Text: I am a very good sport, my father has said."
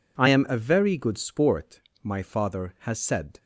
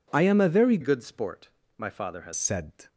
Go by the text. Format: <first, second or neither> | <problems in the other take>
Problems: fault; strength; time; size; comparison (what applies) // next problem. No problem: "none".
first | changes voice from "good" to "has"; from 0.8 to 2.3 s; 1.5 s long